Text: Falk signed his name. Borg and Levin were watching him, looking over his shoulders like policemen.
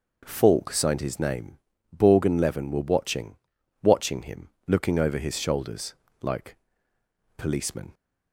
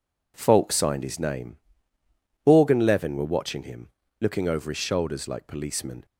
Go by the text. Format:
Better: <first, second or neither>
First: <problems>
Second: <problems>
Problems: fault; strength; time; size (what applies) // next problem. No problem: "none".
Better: second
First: says "watching" twice; at 3.8 s // pauses between "shoulders" and "like"; slight; at 5.9 s; 0.28 s long // pauses between "like" and "policemen"; noticeable; at 6.5 s; 0.80 s long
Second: none